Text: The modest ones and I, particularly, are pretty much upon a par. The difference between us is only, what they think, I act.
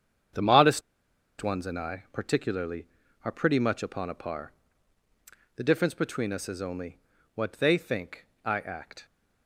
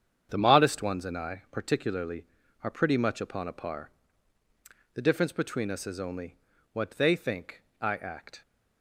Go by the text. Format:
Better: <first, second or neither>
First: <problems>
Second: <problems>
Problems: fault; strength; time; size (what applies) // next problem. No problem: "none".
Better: second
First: starts louder than the rest; strong; until 1.9 s; 8 dB // pauses between "modest" and "ones"; noticeable; at 0.8 s; 0.60 s long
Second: starts louder than the rest; strong; until 1.3 s; 8 dB